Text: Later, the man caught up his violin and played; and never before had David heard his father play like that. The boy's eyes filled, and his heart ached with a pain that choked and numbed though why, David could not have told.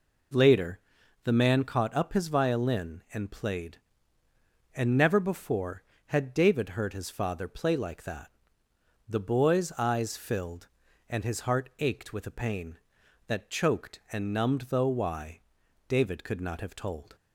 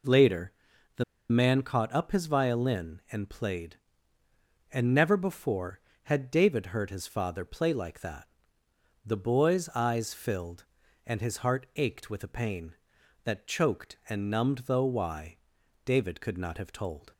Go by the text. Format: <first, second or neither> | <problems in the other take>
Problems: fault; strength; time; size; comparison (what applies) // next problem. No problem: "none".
first | pauses between "the" and "man"; slight; at 1.0 s; 0.26 s long